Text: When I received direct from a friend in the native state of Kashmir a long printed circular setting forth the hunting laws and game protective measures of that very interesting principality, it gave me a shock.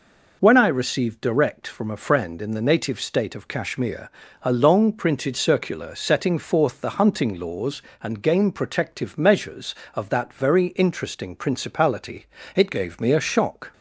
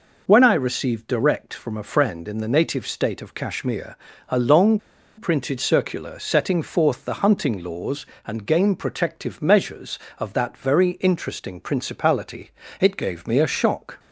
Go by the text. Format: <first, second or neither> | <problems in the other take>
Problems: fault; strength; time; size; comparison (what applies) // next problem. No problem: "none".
first | pauses between "Kashmir" and "a"; slight; at 3.9 s; 0.32 s long; slight in the first // pauses between "long" and "printed"; at 4.7 s; 0.37 s long